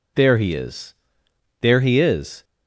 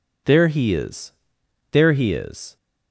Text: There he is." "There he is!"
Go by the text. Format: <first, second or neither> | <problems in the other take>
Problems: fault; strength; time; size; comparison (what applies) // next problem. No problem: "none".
neither | none